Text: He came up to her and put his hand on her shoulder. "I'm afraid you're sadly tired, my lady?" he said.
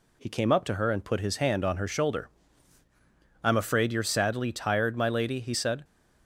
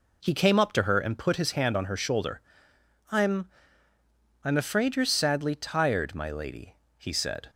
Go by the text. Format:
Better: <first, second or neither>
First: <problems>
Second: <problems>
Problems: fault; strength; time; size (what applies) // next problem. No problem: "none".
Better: first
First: none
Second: says "I'm" twice; at 4.4 s